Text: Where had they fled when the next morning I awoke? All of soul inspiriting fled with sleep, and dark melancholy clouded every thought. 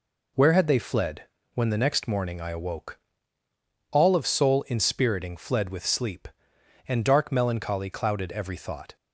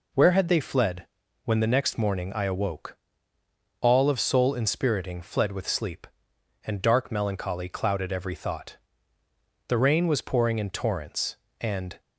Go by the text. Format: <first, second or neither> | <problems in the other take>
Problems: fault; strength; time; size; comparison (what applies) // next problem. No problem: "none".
first | pauses between "fled" and "when"; at 1.0 s; 0.40 s long; slight in the first // goes on to say "The rain was pouring in torrents and"; strong; from 9.6 s on; 2.3 s long